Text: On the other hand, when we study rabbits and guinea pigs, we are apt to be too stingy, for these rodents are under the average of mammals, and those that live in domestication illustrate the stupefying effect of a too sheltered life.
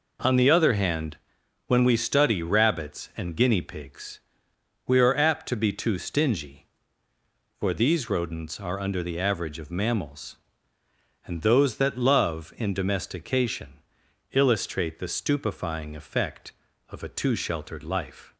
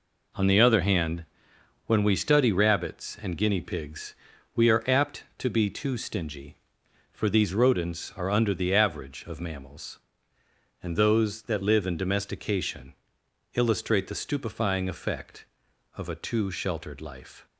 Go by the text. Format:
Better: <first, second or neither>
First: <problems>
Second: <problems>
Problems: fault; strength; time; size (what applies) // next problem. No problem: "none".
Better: second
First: says "love" for "live"; at 11.9 s // pauses between "domestication" and "illustrate"; noticeable; at 13.8 s; 0.52 s long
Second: pauses between "domestication" and "illustrate"; noticeable; at 12.9 s; 0.60 s long